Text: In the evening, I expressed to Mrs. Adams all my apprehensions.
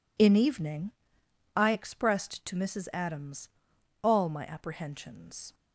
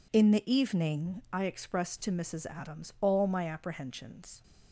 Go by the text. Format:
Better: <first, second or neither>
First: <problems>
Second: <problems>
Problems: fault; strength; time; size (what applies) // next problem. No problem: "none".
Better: second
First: skips "the"; at 0.3 s // pauses between "Adams" and "all"; noticeable; at 3.4 s; 0.52 s long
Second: none